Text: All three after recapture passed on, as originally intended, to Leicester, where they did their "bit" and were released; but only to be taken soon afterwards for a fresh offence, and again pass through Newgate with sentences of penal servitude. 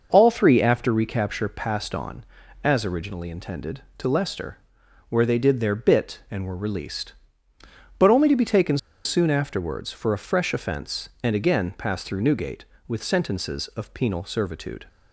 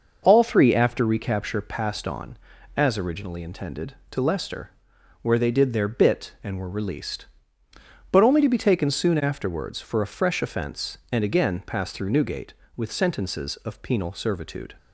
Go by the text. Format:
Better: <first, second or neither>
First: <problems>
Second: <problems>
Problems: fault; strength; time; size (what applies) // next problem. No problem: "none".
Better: second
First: pauses between "taken" and "soon"; slight; at 8.7 s; 0.28 s long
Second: none